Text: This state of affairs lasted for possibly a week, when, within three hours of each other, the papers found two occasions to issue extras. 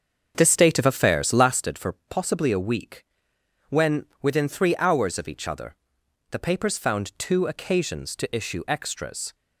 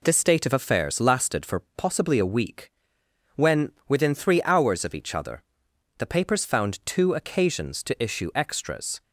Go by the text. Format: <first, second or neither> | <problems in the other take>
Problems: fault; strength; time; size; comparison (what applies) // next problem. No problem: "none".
second | starts louder than the rest; until 1.6 s; 7 dB // pauses between "for" and "possibly"; slight; at 1.9 s; 0.16 s long; slight in the second